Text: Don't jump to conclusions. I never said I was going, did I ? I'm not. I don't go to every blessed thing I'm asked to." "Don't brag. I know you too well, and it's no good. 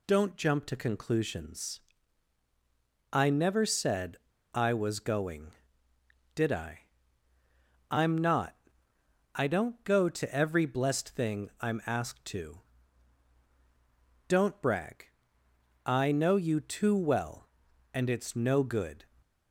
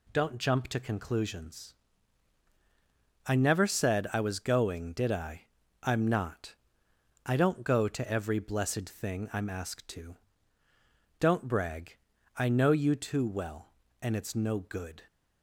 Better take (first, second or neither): second